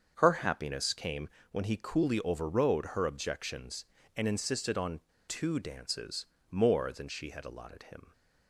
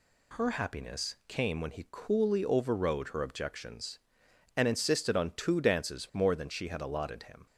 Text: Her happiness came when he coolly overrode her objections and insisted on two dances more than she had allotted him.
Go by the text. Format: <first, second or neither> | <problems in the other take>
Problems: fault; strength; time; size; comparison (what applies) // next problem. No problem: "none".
second | starts louder than the rest; until 1.1 s; 7 dB // pauses between "came" and "when"; slight; at 1.2 s; 0.22 s long // pauses between "on" and "two"; slight; at 5.0 s; 0.27 s long // pauses between "dances" and "more"; slight; at 6.2 s; 0.24 s long